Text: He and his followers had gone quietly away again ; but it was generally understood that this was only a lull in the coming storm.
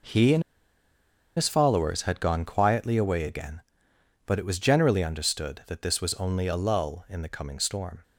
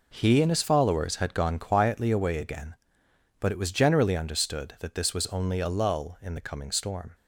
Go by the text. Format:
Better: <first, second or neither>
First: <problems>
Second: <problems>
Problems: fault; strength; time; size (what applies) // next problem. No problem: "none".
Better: second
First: pauses between "and" and "his"; noticeable; at 0.4 s; 0.94 s long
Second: none